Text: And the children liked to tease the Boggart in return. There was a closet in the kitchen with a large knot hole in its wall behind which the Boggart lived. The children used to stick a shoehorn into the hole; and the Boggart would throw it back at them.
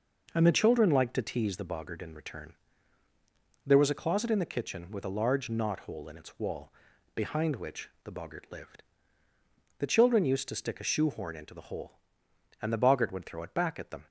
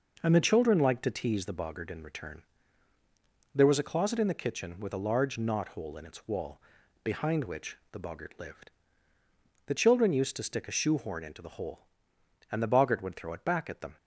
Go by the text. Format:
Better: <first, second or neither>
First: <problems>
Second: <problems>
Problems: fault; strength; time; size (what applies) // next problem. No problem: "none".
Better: neither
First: pauses between "wall" and "behind"; at 6.7 s; 0.44 s long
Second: pauses between "wall" and "behind"; at 6.5 s; 0.44 s long